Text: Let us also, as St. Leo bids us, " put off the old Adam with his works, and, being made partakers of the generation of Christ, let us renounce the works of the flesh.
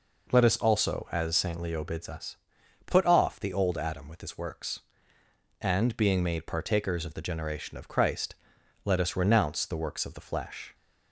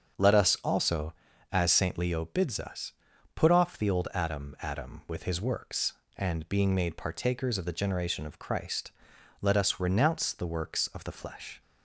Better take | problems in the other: first | starts louder than the rest; strong; until 1.6 s; 7 dB // says "Adam" twice; at 4.6 s

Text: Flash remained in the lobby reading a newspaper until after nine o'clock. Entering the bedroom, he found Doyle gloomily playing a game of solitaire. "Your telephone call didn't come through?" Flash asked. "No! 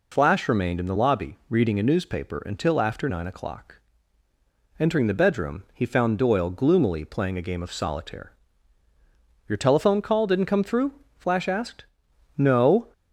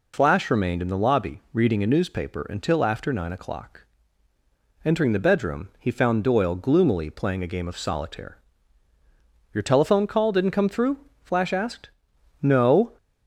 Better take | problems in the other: neither | none

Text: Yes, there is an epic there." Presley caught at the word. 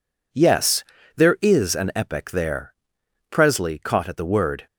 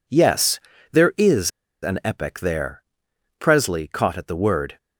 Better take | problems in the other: first | pauses between "is" and "an"; slight; at 1.5 s; 0.32 s long

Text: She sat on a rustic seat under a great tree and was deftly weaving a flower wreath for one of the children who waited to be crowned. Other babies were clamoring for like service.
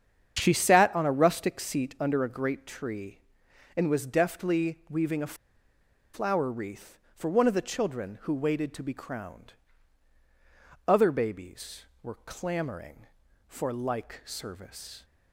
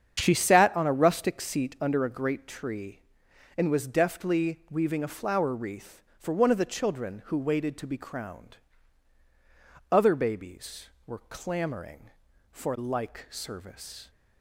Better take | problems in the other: second | starts louder than the rest; strong; until 1.3 s; 8 dB; strong in the second // pauses between "a" and "flower"; noticeable; at 5.3 s; 0.80 s long

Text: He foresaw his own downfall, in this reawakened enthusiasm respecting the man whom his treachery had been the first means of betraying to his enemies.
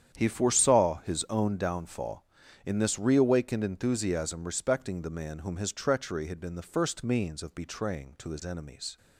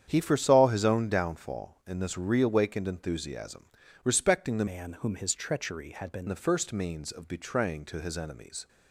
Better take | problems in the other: first | starts louder than the rest; strong; until 1.0 s; 9 dB; strong in the first // pauses between "enthusiasm" and "respecting"; slight; at 3.6 s; 0.36 s long // changes voice from "man" to "been"; from 4.6 to 6.2 s; 1.6 s long

